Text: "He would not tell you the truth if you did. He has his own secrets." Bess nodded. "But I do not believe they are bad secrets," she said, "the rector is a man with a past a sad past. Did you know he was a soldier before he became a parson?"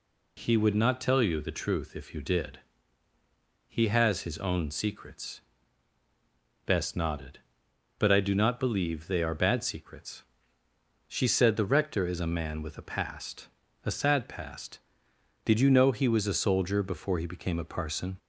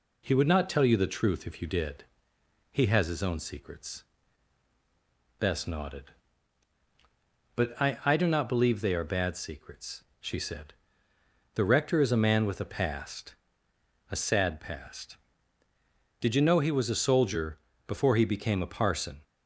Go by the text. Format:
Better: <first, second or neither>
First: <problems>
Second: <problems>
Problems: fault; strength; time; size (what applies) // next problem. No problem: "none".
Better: first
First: pauses between "past" and "a"; slight; at 13.4 s; 0.36 s long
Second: says "I" twice; at 8.0 s // pauses between "past" and "a"; noticeable; at 13.3 s; 0.76 s long // pauses between "soldier" and "before"; slight; at 17.5 s; 0.28 s long